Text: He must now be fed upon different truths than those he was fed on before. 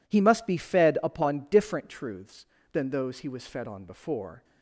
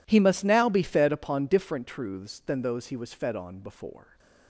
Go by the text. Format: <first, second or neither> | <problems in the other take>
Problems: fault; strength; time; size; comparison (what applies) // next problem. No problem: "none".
second | skips "now"; at 0.4 s